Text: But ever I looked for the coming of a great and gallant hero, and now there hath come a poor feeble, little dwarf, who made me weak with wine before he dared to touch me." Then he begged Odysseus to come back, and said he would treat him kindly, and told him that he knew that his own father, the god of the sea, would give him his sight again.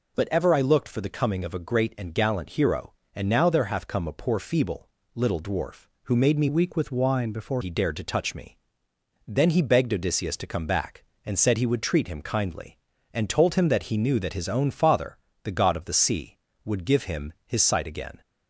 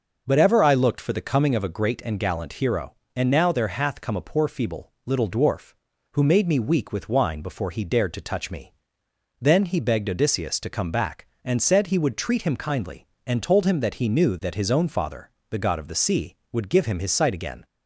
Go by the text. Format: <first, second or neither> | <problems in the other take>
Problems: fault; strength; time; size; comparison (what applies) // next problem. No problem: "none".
second | changes voice from "weak" to "before"; from 6.4 to 7.6 s; 1.2 s long